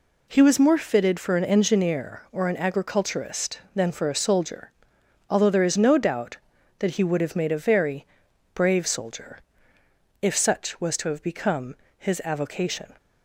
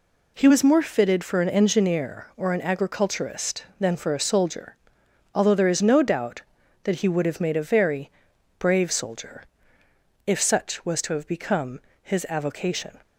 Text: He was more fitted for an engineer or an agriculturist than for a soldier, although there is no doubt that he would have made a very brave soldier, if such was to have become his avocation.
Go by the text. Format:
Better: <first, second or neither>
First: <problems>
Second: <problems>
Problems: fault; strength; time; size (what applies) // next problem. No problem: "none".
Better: neither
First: pauses between "very" and "brave"; noticeable; at 8.0 s; 0.48 s long // pauses between "become" and "his"; slight; at 11.7 s; 0.20 s long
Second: pauses between "very" and "brave"; noticeable; at 8.0 s; 0.48 s long // pauses between "become" and "his"; slight; at 11.8 s; 0.20 s long